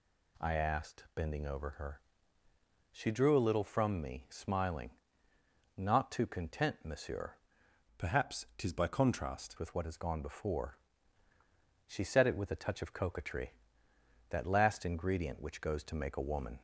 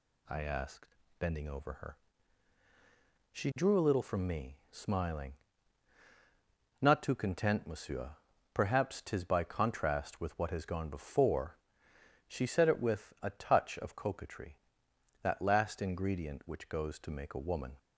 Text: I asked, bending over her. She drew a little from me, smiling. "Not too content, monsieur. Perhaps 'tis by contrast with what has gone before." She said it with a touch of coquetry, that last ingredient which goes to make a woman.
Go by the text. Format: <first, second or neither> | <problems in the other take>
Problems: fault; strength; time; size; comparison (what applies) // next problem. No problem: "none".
second | changes voice from "Perhaps" to "contrast"; from 7.9 to 9.5 s; 1.6 s long